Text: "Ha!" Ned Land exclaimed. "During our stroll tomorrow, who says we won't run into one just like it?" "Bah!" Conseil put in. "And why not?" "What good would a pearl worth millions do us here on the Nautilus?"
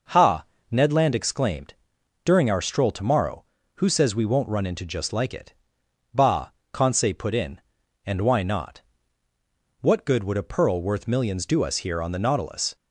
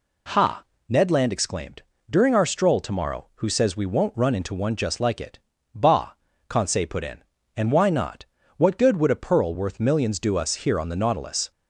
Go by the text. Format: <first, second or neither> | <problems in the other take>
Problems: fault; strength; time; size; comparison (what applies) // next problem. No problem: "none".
second | skips "one"; at 4.8 s